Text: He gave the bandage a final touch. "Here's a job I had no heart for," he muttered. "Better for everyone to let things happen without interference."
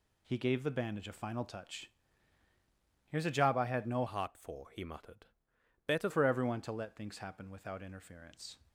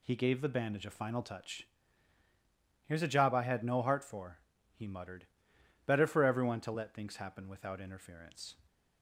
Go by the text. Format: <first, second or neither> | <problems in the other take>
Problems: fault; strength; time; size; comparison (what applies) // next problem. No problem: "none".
second | changes voice from "heart" to "Better"; from 4.0 to 6.0 s; 2.0 s long